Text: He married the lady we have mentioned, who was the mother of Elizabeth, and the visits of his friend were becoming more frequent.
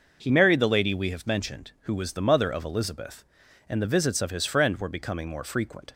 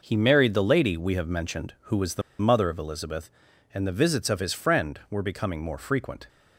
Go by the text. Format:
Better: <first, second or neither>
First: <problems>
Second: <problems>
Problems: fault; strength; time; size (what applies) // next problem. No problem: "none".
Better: first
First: none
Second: pauses between "the" and "mother"; slight; at 2.2 s; 0.19 s long